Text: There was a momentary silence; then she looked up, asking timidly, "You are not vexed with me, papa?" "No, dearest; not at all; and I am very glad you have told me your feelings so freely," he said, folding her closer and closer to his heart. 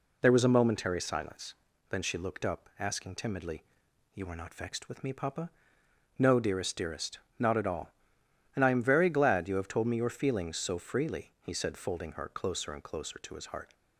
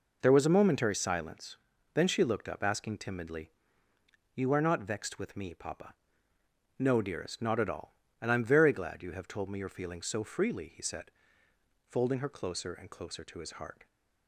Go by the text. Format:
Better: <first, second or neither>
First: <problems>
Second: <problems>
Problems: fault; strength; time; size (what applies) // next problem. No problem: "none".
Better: second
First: says "dearest" twice; at 6.7 s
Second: none